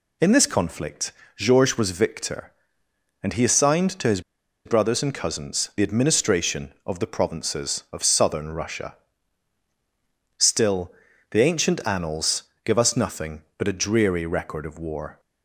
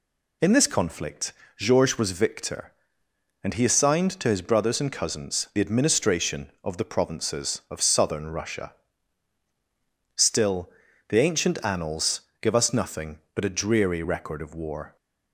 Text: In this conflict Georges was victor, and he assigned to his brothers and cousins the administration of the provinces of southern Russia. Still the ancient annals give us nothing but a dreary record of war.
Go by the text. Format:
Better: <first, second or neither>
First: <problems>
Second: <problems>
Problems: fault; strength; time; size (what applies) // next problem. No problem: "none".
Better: second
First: pauses between "conflict" and "Georges"; slight; at 1.1 s; 0.24 s long // pauses between "his" and "brothers"; at 4.2 s; 0.44 s long // pauses between "Still" and "the"; at 10.8 s; 0.40 s long // pauses between "annals" and "give"; slight; at 12.4 s; 0.22 s long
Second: pauses between "conflict" and "Georges"; slight; at 1.3 s; 0.24 s long // pauses between "Still" and "the"; at 10.6 s; 0.40 s long // pauses between "annals" and "give"; slight; at 12.2 s; 0.20 s long